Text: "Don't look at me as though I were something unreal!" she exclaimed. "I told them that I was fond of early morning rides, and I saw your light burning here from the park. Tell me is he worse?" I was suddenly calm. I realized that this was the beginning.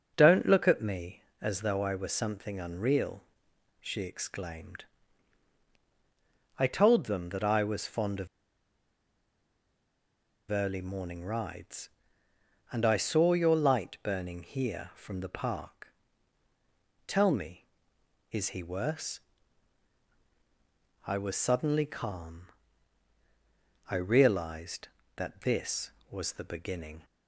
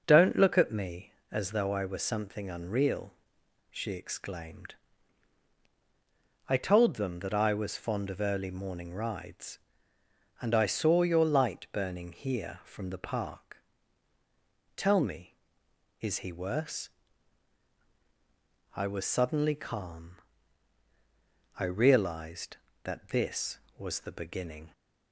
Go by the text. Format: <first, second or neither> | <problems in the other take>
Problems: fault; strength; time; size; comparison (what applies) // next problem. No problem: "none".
second | starts louder than the rest; noticeable; until 1.1 s; 6 dB; noticeable in the second // pauses between "of" and "early"; strong; at 8.2 s; 2.2 s long